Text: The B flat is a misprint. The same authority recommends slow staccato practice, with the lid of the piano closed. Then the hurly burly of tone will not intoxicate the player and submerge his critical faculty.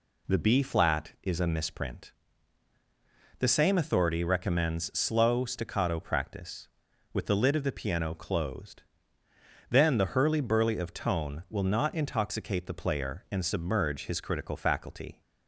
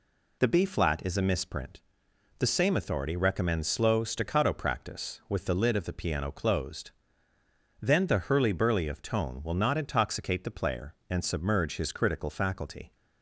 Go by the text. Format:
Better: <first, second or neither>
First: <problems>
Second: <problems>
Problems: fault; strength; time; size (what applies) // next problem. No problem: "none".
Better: neither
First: none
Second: none